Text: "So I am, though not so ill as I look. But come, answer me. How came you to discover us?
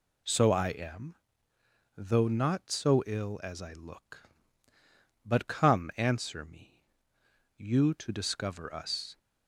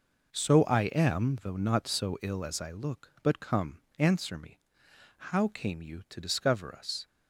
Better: second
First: skips "How came"; at 7.2 s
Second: none

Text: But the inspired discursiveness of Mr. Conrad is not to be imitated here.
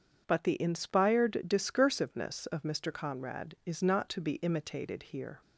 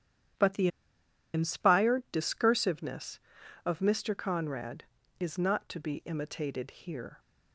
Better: first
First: starts louder than the rest; strong; until 1.2 s; 7.5 dB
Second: starts louder than the rest; strong; until 2.0 s; 10.5 dB // pauses between "the" and "inspired"; noticeable; at 0.6 s; 0.66 s long

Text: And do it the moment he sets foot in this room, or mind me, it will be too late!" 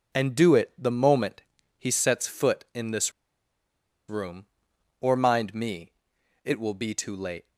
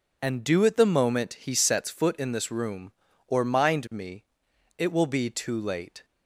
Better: second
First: pauses between "moment" and "he"; slight; at 1.4 s; 0.36 s long // pauses between "this" and "room"; noticeable; at 3.1 s; 0.96 s long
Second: none

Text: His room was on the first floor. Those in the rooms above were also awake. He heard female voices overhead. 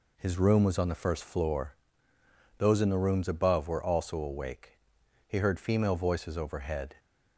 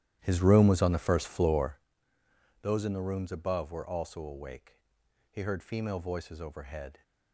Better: first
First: none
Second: starts louder than the rest; strong; until 1.8 s; 12.5 dB

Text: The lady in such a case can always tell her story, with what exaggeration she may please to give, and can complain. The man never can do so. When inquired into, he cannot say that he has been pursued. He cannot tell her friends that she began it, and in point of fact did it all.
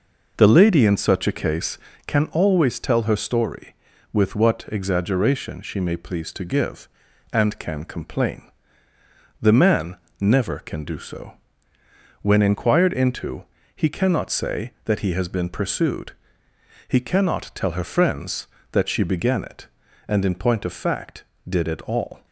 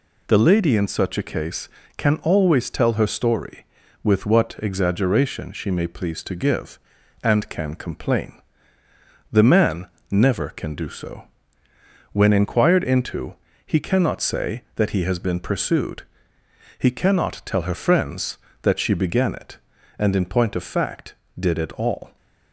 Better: second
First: starts louder than the rest; noticeable; until 2.2 s; 5 dB // pauses between "man" and "never"; slight; at 9.9 s; 0.24 s long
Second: pauses between "man" and "never"; slight; at 9.8 s; 0.24 s long

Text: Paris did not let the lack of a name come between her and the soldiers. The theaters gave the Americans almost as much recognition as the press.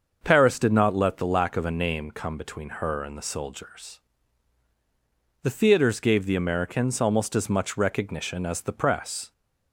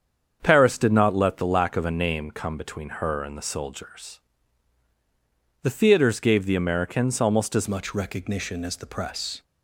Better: first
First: starts louder than the rest; until 1.2 s; 6.5 dB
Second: starts louder than the rest; strong; until 1.4 s; 7.5 dB // changes voice at "much"; from 7.6 s on; 1.8 s long

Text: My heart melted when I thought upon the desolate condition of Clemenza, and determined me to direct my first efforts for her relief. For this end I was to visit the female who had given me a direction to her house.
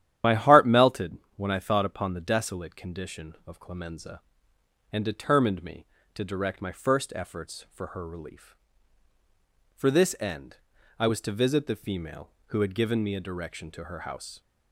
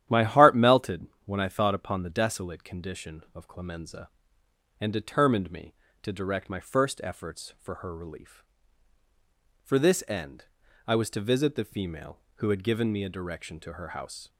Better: second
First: loses the start of "My"; at 0.2 s; 35 ms // starts louder than the rest; strong; until 1.4 s; 11 dB // pauses between "melted" and "when"; slight; at 1.1 s; 0.22 s long // pauses between "end" and "I"; at 10.5 s; 0.40 s long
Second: starts louder than the rest; strong; until 1.3 s; 11 dB // pauses between "melted" and "when"; slight; at 1.0 s; 0.22 s long // pauses between "end" and "I"; at 10.4 s; 0.40 s long

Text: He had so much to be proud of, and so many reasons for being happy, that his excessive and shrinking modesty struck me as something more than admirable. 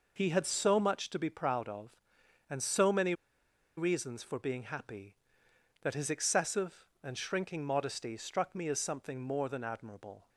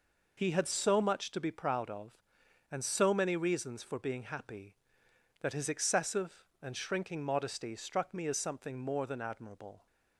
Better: second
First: pauses between "many" and "reasons"; noticeable; at 3.1 s; 0.64 s long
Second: none

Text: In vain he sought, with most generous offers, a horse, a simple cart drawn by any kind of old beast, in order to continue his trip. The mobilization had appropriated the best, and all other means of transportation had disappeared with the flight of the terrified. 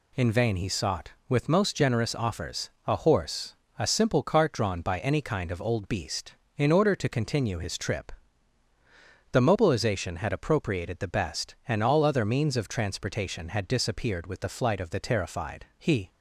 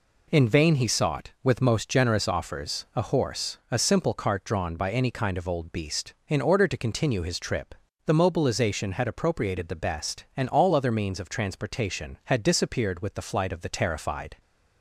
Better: second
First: goes on to say "He"; slight; from 15.7 s on; 0.30 s long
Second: none

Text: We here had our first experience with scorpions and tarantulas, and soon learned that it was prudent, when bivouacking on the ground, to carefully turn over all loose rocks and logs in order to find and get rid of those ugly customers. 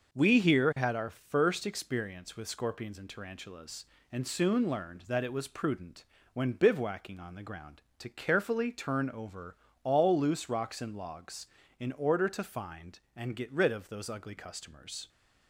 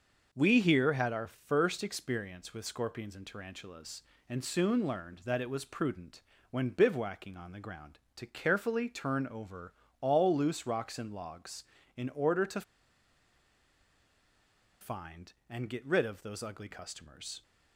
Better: first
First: starts louder than the rest; noticeable; until 1.1 s; 6 dB // pauses between "over" and "all"; slight; at 9.5 s; 0.26 s long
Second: starts louder than the rest; noticeable; until 1.3 s; 6 dB // pauses between "over" and "all"; slight; at 9.7 s; 0.26 s long // pauses between "to" and "find"; strong; at 12.6 s; 2.1 s long

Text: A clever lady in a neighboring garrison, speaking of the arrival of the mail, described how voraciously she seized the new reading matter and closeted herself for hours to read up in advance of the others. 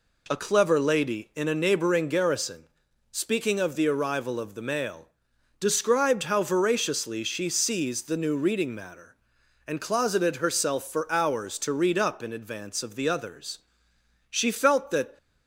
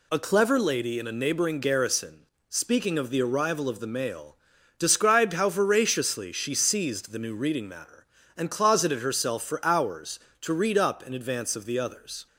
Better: second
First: goes on to say "She felt that"; noticeable; from 14.2 s on; 0.88 s long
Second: none

